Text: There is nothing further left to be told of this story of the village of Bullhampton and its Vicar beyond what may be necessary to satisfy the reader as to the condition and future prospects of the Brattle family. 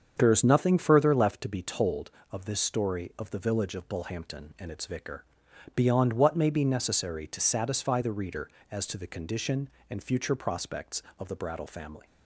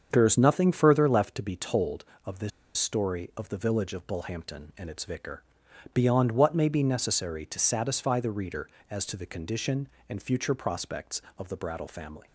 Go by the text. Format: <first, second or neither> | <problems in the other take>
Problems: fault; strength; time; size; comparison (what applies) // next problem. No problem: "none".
first | starts louder than the rest; strong; until 1.1 s; 7 dB; strong in the first // pauses between "this" and "story"; slight; at 2.5 s; 0.27 s long // pauses between "Vicar" and "beyond"; noticeable; at 5.4 s; 0.52 s long; noticeable in the first